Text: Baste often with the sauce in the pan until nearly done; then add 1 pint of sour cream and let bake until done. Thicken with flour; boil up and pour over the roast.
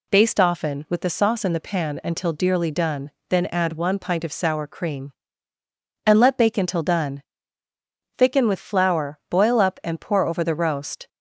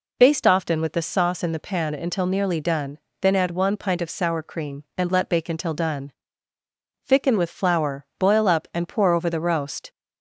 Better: second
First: says "dearly" for "nearly"; at 2.3 s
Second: none

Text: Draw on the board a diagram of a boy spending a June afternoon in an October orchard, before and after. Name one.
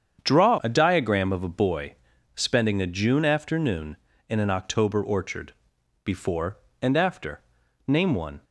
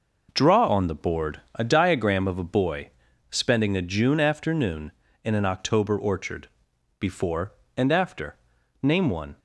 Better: second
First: starts louder than the rest; strong; until 1.2 s; 8 dB // skips "on the board"; at 0.5 s // pauses between "boy" and "spending"; at 1.9 s; 0.42 s long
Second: pauses between "boy" and "spending"; at 2.8 s; 0.42 s long

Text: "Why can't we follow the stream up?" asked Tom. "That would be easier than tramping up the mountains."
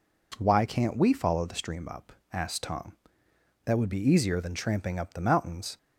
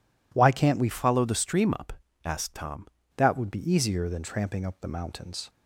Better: first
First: none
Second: changes voice from "follow" to "Tom"; from 0.9 to 2.8 s; 1.9 s long

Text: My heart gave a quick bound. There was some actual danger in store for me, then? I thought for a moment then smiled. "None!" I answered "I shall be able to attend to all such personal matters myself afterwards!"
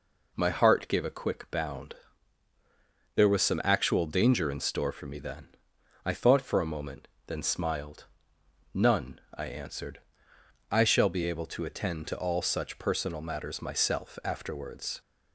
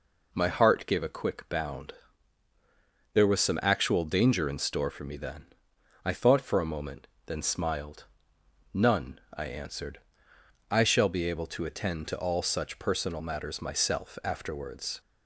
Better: neither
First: pauses between "moment" and "then"; slight; at 7.0 s; 0.18 s long // pauses between "answered" and "I"; noticeable; at 9.9 s; 0.72 s long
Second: pauses between "moment" and "then"; slight; at 7.0 s; 0.18 s long // pauses between "answered" and "I"; noticeable; at 9.9 s; 0.72 s long

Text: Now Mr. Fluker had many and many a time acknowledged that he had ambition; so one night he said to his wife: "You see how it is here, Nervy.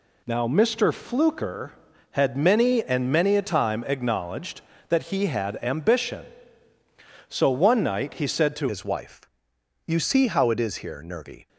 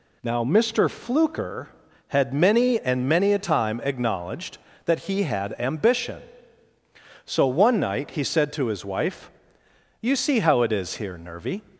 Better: second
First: changes voice at "his"; from 8.7 s on; 2.7 s long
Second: none

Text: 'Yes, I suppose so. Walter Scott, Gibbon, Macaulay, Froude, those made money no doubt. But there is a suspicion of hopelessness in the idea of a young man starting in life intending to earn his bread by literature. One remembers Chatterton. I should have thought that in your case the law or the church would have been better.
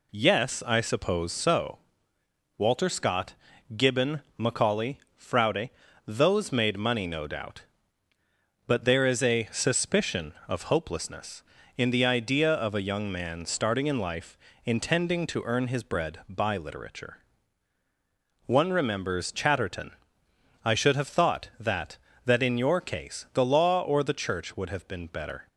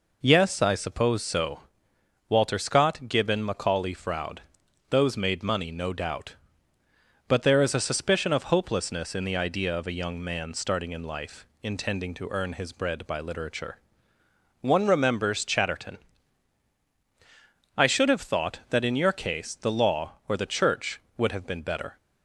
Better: second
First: pauses between "life" and "intending"; slight; at 14.3 s; 0.26 s long // says "that" twice; at 22.2 s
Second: pauses between "life" and "intending"; slight; at 11.4 s; 0.16 s long

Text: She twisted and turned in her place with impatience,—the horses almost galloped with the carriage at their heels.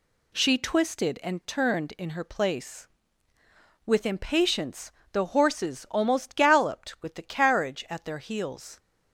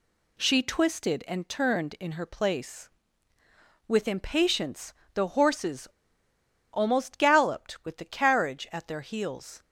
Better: first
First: none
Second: pauses between "horses" and "almost"; noticeable; at 5.8 s; 0.84 s long

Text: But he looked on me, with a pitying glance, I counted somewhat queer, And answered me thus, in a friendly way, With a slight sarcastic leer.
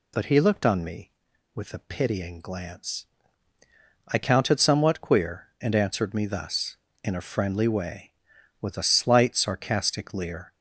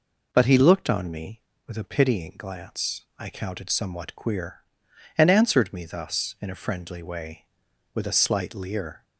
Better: first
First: none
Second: skips "sarcastic"; at 8.5 s

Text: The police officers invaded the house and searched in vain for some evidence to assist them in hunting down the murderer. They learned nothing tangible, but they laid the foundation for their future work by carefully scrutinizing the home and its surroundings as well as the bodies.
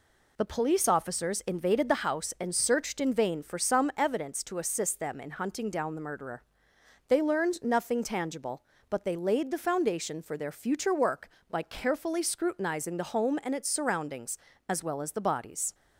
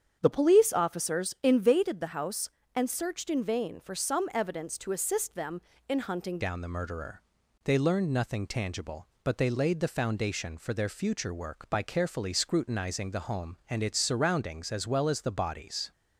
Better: first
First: none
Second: starts louder than the rest; strong; until 1.2 s; 7.5 dB // changes voice at "down"; from 6.4 s on; 9.5 s long

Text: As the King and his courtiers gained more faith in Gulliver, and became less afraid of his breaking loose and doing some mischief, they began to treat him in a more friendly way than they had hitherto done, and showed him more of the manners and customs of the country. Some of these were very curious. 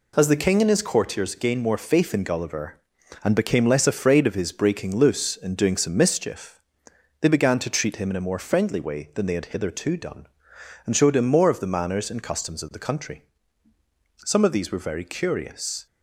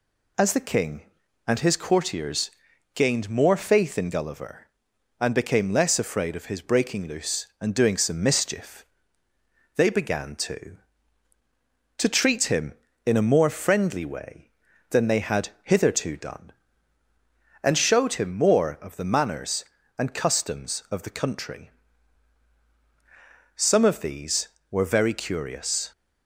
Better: first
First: none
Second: pauses between "courtiers" and "gained"; at 2.5 s; 0.44 s long // says "to" twice; at 11.9 s // pauses between "had" and "hitherto"; slight; at 15.4 s; 0.16 s long

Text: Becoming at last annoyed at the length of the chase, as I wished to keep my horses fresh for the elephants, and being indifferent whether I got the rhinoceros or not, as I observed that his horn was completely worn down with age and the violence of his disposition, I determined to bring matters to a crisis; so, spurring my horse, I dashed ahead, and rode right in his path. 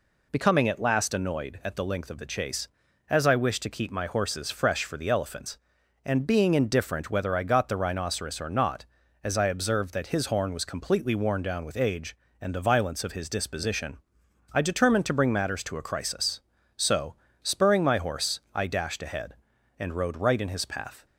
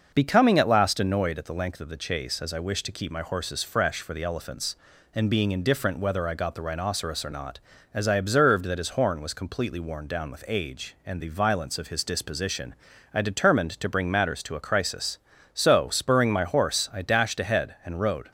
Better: first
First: none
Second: starts louder than the rest; noticeable; until 1.1 s; 6 dB // stops before "right in his path"; at 18.2 s

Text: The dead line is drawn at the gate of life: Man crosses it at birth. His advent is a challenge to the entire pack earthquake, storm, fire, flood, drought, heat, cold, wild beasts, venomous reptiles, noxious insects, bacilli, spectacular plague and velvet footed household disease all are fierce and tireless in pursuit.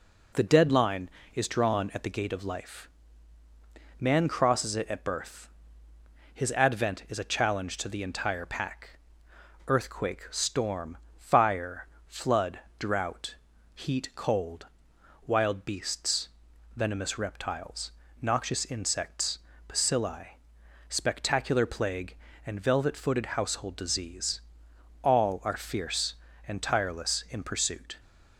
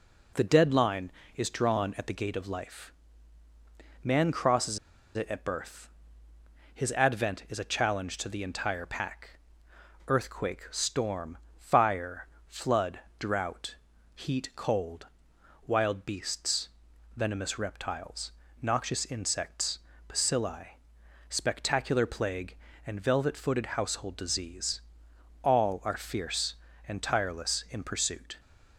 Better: first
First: pauses between "pack" and "earthquake"; noticeable; at 8.9 s; 0.68 s long // pauses between "disease" and "all"; noticeable; at 24.4 s; 0.60 s long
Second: pauses between "crosses" and "it"; at 4.7 s; 0.37 s long // pauses between "pack" and "earthquake"; noticeable; at 9.3 s; 0.68 s long // pauses between "disease" and "all"; noticeable; at 24.8 s; 0.60 s long

